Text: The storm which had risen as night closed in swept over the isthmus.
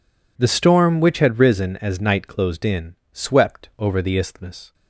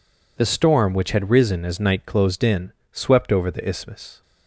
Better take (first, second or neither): neither